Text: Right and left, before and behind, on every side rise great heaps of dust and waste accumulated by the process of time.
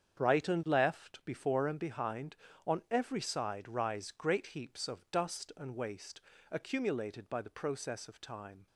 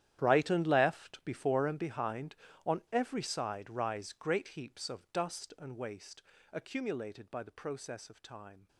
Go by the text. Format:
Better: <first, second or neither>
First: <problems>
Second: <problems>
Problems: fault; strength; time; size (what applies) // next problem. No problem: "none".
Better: first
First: starts louder than the rest; strong; until 1.2 s; 8 dB // pauses between "waste" and "accumulated"; slight; at 6.2 s; 0.32 s long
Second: gets quieter; strong; throughout; 16.5 dB // starts louder than the rest; strong; until 1.2 s; 11 dB // pauses between "waste" and "accumulated"; slight; at 6.2 s; 0.32 s long